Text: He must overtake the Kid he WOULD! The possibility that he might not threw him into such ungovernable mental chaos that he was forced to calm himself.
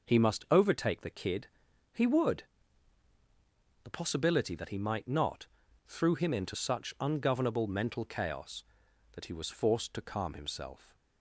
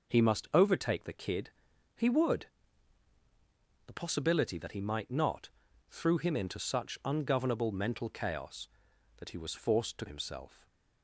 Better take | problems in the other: first | pauses between "Kid" and "he"; noticeable; at 1.4 s; 0.46 s long; noticeable in the first // pauses between "not" and "threw"; at 5.4 s; 0.40 s long; also in the first // skips "calm"; at 10.0 s

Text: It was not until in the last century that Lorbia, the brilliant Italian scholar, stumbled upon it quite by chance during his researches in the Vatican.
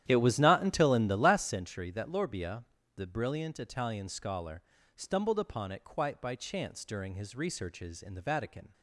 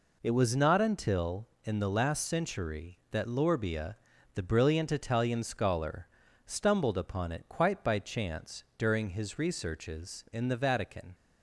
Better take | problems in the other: second | starts louder than the rest; strong; until 1.6 s; 11 dB

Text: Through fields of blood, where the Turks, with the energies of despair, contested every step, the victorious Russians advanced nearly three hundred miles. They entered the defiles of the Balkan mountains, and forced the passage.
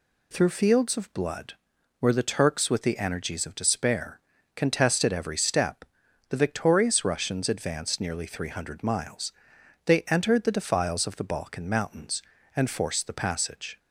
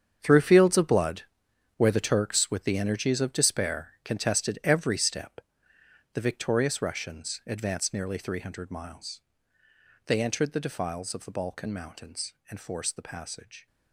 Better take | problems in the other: first | gets quieter; strong; throughout; 13.5 dB

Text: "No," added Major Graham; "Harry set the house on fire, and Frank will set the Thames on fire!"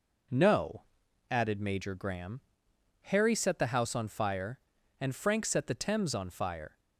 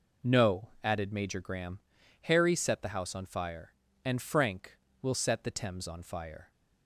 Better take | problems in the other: second | skips "will"; at 5.4 s

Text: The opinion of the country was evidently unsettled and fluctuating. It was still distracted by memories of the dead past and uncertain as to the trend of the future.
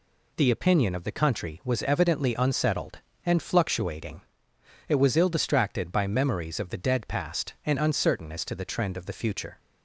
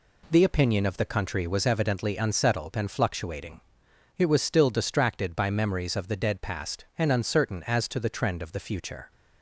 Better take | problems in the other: second | says "ill" for "still"; at 5.1 s

